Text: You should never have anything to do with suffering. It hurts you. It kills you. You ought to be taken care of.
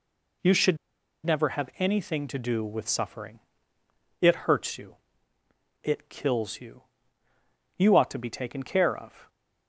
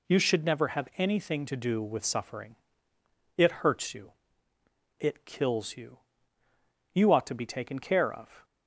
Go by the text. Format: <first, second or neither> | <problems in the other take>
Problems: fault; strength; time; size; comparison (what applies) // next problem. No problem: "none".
second | pauses between "should" and "never"; noticeable; at 0.7 s; 0.47 s long